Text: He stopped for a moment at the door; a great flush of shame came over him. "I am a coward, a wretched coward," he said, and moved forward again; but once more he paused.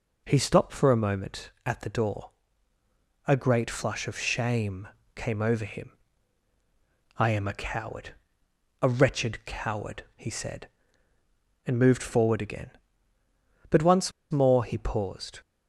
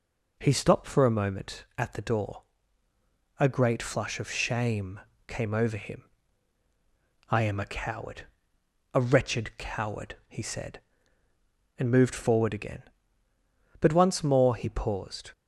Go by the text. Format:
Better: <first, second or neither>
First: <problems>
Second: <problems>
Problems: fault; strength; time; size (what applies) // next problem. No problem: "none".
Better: second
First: pauses between "shame" and "came"; slight; at 4.8 s; 0.28 s long // pauses between "once" and "more"; slight; at 14.1 s; 0.21 s long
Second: pauses between "shame" and "came"; slight; at 4.9 s; 0.28 s long